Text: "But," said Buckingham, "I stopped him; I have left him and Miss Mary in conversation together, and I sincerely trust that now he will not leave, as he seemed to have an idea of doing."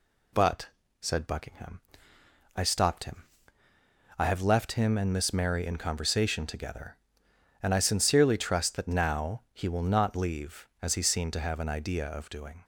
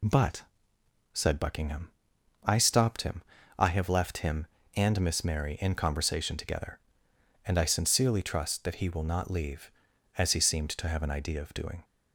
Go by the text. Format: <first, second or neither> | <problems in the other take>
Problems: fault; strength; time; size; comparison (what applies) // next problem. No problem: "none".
first | skips "now"; at 8.7 s